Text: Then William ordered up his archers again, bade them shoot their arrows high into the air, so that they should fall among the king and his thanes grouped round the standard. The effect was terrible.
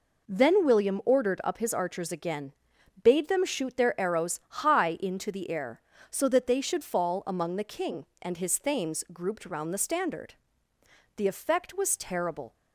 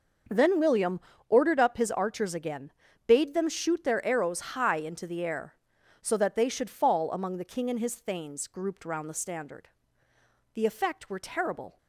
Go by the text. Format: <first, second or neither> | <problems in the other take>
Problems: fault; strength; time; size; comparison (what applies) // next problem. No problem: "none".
first | pauses between "William" and "ordered"; slight; at 0.9 s; 0.30 s long // says "were" for "was"; at 11.0 s